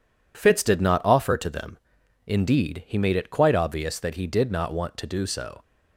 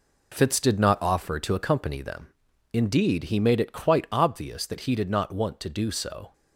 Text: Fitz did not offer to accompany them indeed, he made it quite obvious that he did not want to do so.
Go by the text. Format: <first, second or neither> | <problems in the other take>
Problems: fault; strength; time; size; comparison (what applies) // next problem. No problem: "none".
second | skips "accompany"; at 1.4 s // pauses between "them" and "indeed"; noticeable; at 1.7 s; 0.48 s long; noticeable in the second